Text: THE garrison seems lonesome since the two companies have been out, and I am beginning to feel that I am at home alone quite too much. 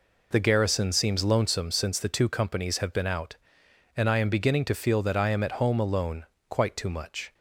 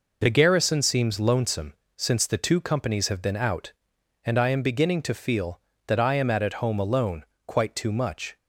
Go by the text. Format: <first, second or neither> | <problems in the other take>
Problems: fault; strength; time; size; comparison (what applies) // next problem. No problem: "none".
first | pauses between "lonesome" and "since"; slight; at 1.7 s; 0.24 s long // says "at" twice; at 6.4 s // pauses between "alone" and "quite"; slight; at 7.2 s; 0.22 s long; slight in the first